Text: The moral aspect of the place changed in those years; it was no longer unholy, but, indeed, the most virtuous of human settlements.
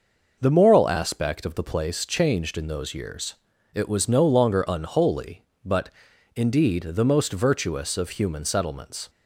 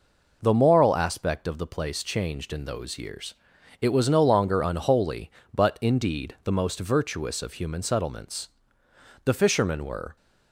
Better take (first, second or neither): first